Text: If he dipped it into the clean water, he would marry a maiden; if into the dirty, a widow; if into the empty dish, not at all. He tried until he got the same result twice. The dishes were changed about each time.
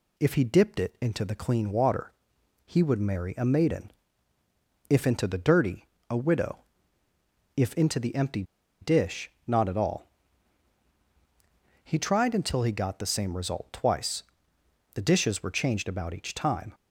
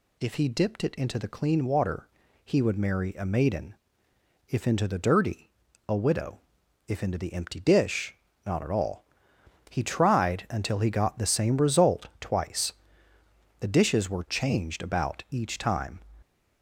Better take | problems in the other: second | pauses between "empty" and "dish"; at 8.4 s; 0.38 s long

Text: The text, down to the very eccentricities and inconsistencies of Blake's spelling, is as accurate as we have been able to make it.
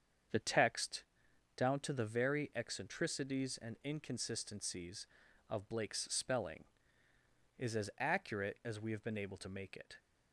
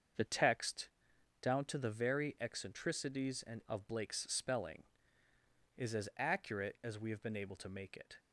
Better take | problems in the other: first | starts louder than the rest; until 1.7 s; 6.5 dB; strong in the first // skips "inconsistencies"; at 3.6 s

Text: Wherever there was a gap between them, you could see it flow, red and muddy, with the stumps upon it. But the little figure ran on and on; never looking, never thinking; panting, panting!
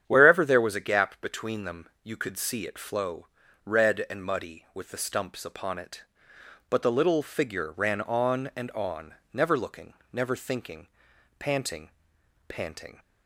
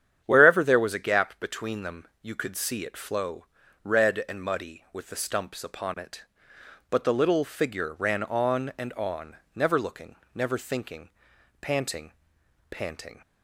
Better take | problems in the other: neither | starts louder than the rest; strong; the same in both

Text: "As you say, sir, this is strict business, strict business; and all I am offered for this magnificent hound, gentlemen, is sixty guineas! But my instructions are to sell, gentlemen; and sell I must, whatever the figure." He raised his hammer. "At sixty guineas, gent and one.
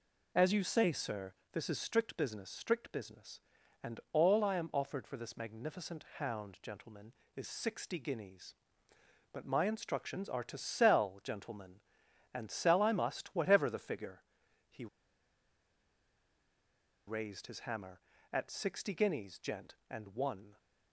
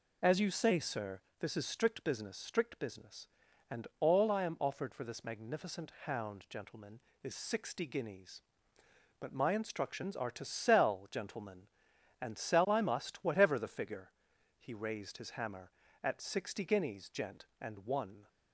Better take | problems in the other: second | pauses between "He" and "raised"; strong; at 14.8 s; 2.2 s long

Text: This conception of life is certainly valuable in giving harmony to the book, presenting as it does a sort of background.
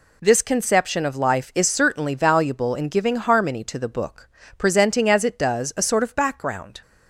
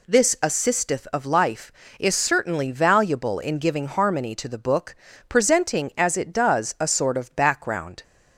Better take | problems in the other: first | says "assisteth" for "conception"; at 0.4 s

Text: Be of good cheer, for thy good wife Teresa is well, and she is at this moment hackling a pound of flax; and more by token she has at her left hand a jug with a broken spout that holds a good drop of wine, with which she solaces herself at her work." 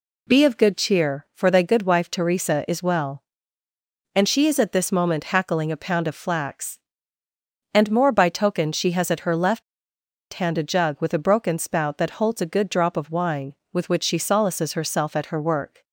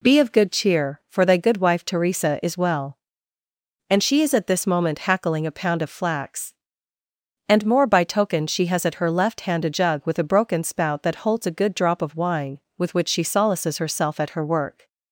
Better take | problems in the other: second | pauses between "left" and "hand"; noticeable; at 9.6 s; 0.70 s long

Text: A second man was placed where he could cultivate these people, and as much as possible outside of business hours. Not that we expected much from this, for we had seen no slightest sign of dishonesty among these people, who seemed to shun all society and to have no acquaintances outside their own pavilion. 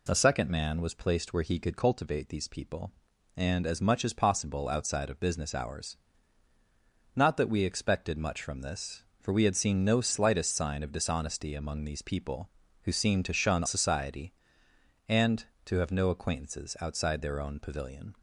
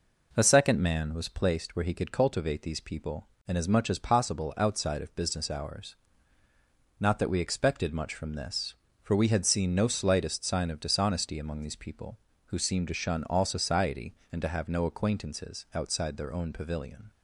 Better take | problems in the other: second | skips "all"; at 13.6 s

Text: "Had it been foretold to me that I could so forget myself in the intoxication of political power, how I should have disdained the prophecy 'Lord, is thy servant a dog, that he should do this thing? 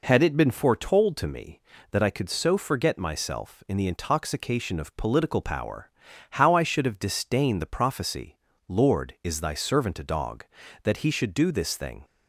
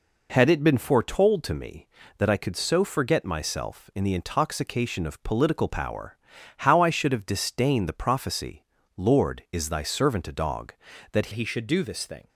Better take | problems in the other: first | pauses between "prophecy" and "Lord"; slight; at 8.6 s; 0.32 s long; slight in the first // changes voice at "he"; from 11.3 s on; 0.9 s long

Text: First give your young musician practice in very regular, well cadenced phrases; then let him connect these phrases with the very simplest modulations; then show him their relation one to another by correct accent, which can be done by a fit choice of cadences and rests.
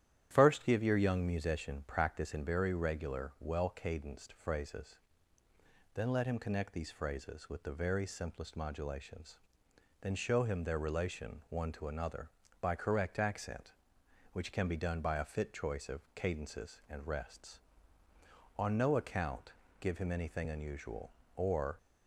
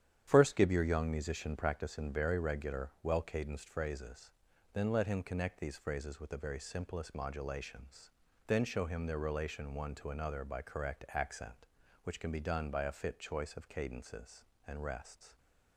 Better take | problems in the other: second | starts louder than the rest; strong; until 1.3 s; 11 dB; strong in the second // goes on to say "On no account give him anything unusual or"; strong; from 18.5 s on; 3.1 s long

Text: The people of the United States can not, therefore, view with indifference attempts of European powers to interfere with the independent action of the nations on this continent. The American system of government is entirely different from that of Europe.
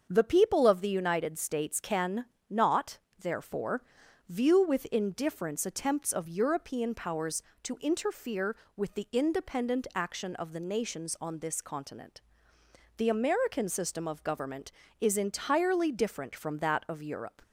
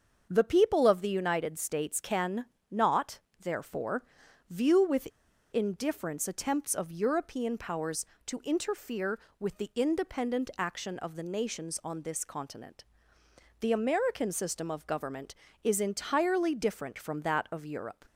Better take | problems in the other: first | starts louder than the rest; until 1.3 s; 6.5 dB; also in the first // pauses between "can" and "not"; slight; at 2.4 s; 0.26 s long; slight in the first // pauses between "with" and "indifference"; at 5.0 s; 0.45 s long

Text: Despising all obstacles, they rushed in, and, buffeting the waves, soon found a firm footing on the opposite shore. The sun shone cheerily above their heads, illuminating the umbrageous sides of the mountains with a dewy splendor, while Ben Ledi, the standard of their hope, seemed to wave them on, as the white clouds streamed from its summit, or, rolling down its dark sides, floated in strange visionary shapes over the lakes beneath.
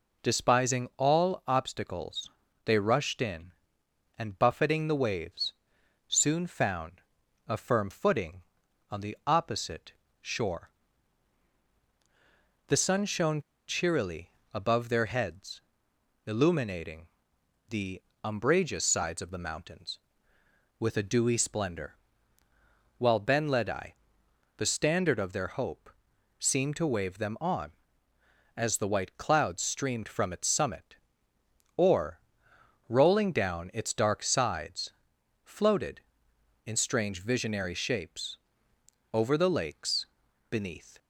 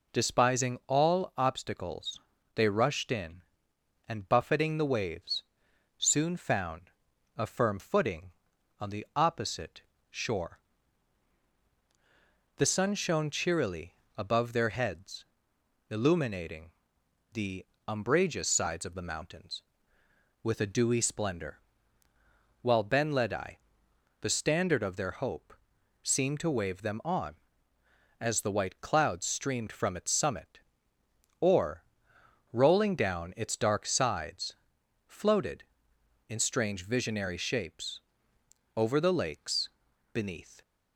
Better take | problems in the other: second | pauses between "found" and "a"; noticeable; at 7.0 s; 0.46 s long; noticeable in the second // pauses between "opposite" and "shore"; slight; at 9.9 s; 0.28 s long; slight in the second // pauses between "shone" and "cheerily"; slight; at 13.4 s; 0.27 s long // pauses between "cheerily" and "above"; slight; at 14.3 s; 0.20 s long; slight in the second // pauses between "illuminating" and "the"; noticeable; at 17.0 s; 0.64 s long; noticeable in the second // pauses between "the" and "umbrageous"; slight; at 18.0 s; 0.20 s long; slight in the second // pauses between "shapes" and "over"; noticeable; at 38.3 s; 0.76 s long; noticeable in the second // pauses between "lakes" and "beneath"; at 40.0 s; 0.44 s long; also in the second

